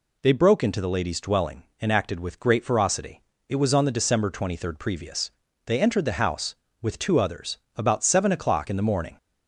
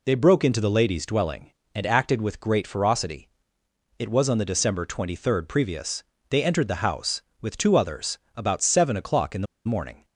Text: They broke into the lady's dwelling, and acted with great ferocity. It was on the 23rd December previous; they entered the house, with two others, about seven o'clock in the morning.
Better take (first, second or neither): first